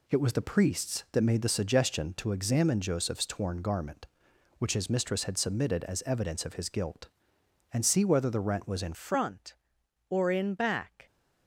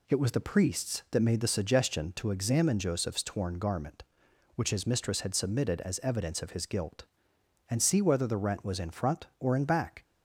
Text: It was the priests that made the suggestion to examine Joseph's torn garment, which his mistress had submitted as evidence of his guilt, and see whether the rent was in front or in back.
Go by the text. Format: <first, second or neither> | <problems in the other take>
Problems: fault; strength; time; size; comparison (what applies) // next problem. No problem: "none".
second | changes voice at "front"; from 8.9 s on; 2.1 s long